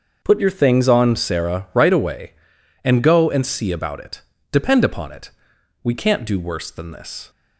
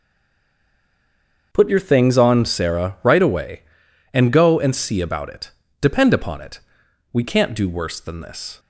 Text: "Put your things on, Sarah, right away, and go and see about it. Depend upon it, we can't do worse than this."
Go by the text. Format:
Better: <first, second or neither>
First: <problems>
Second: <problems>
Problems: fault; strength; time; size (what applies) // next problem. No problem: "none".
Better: first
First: starts louder than the rest; until 1.2 s; 6 dB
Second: stays silent before the first word; noticeable; until 1.5 s; 1.5 s long // starts louder than the rest; until 2.5 s; 6 dB